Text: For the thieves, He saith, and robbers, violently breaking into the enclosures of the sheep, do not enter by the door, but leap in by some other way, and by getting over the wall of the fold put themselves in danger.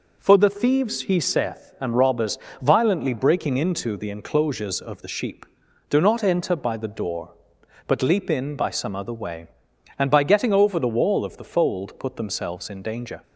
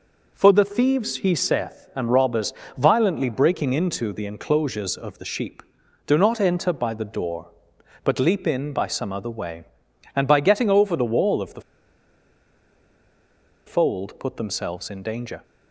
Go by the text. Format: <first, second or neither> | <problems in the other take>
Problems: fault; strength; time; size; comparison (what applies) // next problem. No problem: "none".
first | pauses between "the" and "fold"; strong; at 11.6 s; 2.0 s long